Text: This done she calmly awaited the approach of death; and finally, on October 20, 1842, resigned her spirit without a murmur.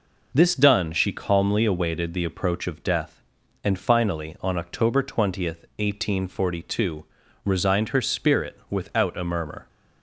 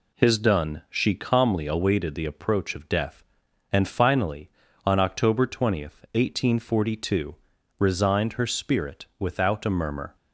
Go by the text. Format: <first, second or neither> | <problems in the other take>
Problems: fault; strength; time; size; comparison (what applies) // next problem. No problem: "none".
first | says "His" for "This"; at 0.1 s